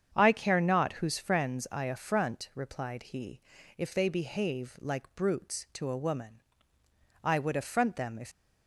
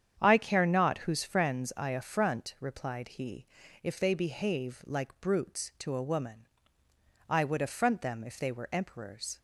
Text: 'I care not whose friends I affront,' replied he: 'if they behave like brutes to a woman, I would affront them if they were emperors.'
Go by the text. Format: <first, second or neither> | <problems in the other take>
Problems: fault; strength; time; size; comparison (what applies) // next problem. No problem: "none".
second | starts louder than the rest; strong; until 1.1 s; 8 dB; strong in the second // stops before "they were emperors"; at 8.3 s